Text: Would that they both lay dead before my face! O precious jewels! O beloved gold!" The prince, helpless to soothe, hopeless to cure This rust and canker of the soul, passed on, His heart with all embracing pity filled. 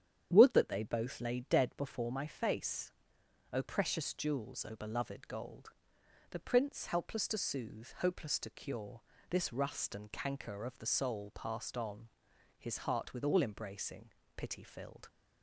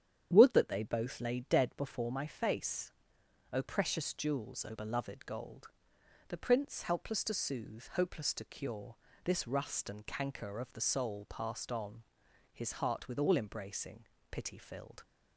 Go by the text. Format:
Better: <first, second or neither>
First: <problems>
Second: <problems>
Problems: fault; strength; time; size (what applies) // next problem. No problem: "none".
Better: neither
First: starts louder than the rest; strong; until 1.3 s; 9 dB // pauses between "cure" and "This"; slight; at 9.0 s; 0.28 s long // pauses between "embracing" and "pity"; slight; at 14.0 s; 0.26 s long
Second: starts louder than the rest; strong; until 1.3 s; 9 dB // pauses between "cure" and "This"; slight; at 8.9 s; 0.28 s long // pauses between "embracing" and "pity"; slight; at 14.0 s; 0.26 s long